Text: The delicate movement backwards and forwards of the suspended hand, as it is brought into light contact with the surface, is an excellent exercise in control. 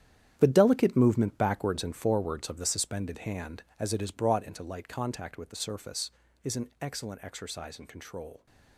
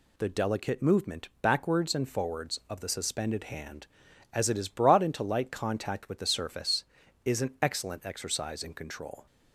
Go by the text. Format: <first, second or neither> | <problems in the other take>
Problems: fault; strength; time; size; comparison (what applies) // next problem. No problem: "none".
second | gets quieter; strong; throughout; 11.5 dB